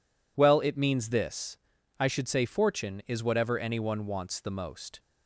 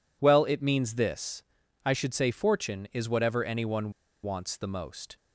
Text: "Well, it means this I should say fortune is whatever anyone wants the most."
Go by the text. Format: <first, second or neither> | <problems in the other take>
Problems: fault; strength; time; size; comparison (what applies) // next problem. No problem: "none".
first | pauses between "this" and "I"; at 1.4 s; 0.42 s long; also in the first // pauses between "anyone" and "wants"; slight; at 3.9 s; 0.31 s long